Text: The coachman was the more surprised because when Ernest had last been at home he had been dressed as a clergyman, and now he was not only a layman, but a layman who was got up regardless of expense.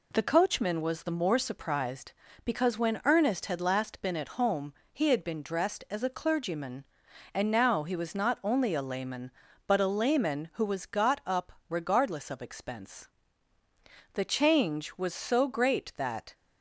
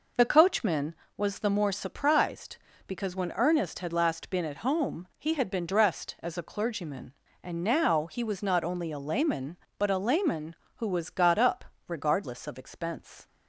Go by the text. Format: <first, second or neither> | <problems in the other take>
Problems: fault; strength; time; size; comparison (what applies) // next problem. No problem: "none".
second | pauses between "home" and "he"; slight; at 4.7 s; 0.18 s long // pauses between "up" and "regardless"; slight; at 11.4 s; 0.20 s long; slight in the second // goes on to say "The change was so great that"; strong; from 14.1 s on; 2.2 s long